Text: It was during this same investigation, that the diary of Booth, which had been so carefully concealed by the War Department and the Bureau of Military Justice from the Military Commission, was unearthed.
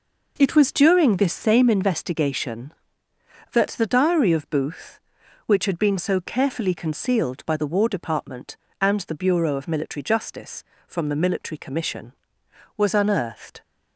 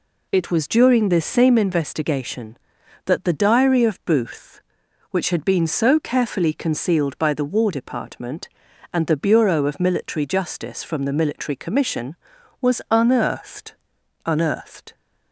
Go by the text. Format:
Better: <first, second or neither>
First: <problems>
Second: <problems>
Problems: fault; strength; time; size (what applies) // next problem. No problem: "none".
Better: first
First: none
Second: says "unearthed" twice; at 14.2 s